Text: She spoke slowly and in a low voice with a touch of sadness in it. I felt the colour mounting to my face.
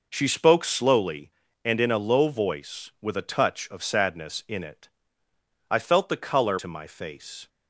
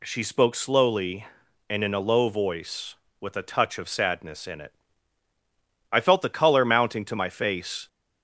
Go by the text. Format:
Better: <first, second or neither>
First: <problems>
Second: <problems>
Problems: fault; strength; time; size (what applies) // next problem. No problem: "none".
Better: second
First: skips "mounting"; at 6.5 s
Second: none